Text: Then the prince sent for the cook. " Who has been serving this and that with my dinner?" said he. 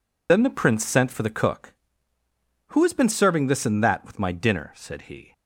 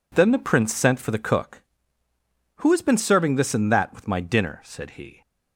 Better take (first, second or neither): second